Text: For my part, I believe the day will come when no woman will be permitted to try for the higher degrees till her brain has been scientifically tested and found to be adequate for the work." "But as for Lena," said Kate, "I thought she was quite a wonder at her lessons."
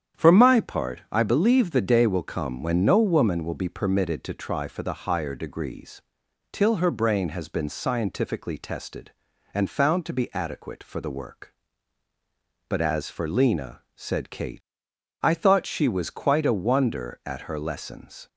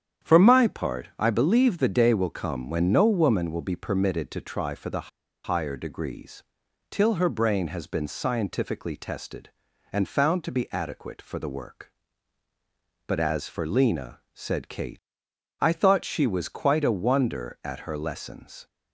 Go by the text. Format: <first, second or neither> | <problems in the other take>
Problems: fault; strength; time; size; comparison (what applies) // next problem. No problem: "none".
first | starts louder than the rest; strong; until 1.3 s; 9 dB; strong in the first // pauses between "the" and "higher"; slight; at 5.0 s; 0.34 s long // pauses between "degrees" and "till"; noticeable; at 6.4 s; 0.48 s long; noticeable in the first